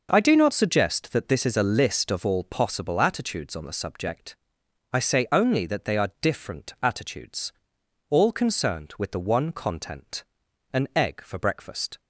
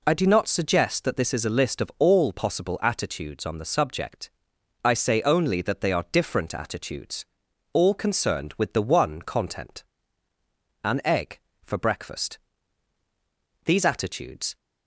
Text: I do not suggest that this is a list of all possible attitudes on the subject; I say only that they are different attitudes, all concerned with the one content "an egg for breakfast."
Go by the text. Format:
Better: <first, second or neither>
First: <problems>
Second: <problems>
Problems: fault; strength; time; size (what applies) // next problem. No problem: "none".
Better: first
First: pauses between "content" and "an"; noticeable; at 10.2 s; 0.50 s long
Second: pauses between "content" and "an"; noticeable; at 9.8 s; 0.98 s long // goes on to say "These attitudes"; noticeable; from 13.6 s on; 0.92 s long